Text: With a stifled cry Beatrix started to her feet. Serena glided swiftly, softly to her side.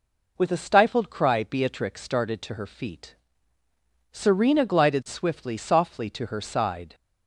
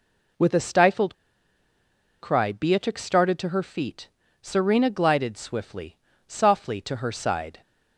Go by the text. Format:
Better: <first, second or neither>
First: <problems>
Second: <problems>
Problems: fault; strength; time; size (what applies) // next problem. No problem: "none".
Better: first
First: none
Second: pauses between "stifled" and "cry"; at 1.1 s; 1.0 s long